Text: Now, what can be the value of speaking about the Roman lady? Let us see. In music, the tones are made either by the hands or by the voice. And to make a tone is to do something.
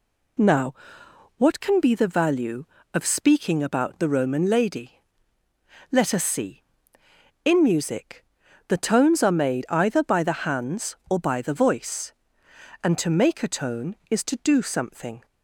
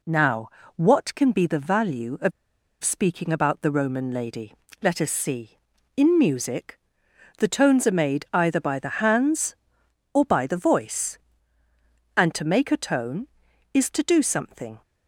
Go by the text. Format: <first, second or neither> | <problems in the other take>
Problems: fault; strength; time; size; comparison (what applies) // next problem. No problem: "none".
first | pauses between "of" and "speaking"; noticeable; at 2.3 s; 0.52 s long